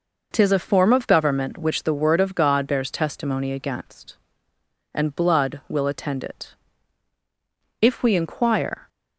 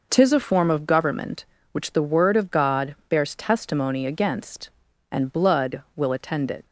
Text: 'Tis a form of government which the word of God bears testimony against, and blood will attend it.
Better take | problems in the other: second | goes on to say "If we inquire"; noticeable; from 7.8 s on; 1.0 s long

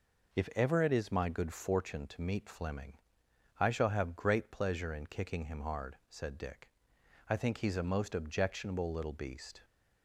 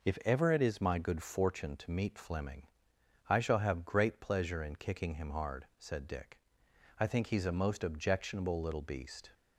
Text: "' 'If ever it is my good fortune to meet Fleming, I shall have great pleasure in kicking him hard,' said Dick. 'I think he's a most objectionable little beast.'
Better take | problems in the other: neither | none

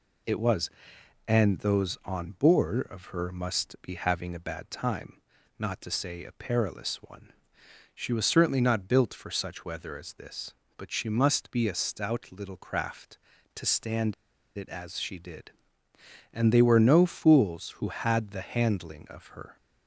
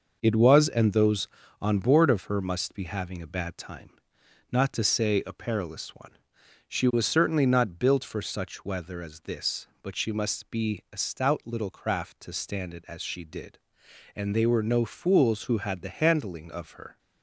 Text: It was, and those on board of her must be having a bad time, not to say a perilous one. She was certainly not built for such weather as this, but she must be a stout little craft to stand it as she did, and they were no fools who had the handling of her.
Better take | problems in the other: second | pauses between "stand" and "it"; at 14.1 s; 0.44 s long

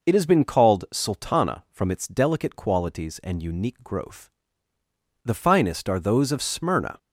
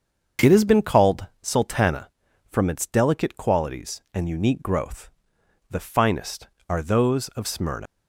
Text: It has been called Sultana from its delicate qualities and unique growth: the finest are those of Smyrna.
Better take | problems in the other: first | starts louder than the rest; until 1.6 s; 7 dB // pauses between "called" and "Sultana"; slight; at 1.2 s; 0.16 s long // leaves "Smyrna" unfinished; at 7.8 s; 145 ms

